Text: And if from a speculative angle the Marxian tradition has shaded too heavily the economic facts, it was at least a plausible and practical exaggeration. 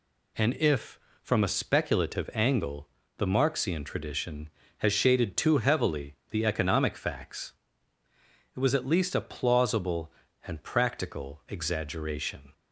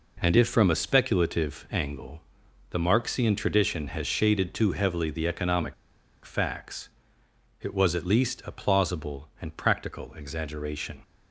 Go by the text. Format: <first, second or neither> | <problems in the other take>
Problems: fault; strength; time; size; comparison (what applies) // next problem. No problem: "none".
first | pauses between "angle" and "the"; noticeable; at 2.2 s; 0.50 s long; slight in the first // pauses between "economic" and "facts"; noticeable; at 5.7 s; 0.51 s long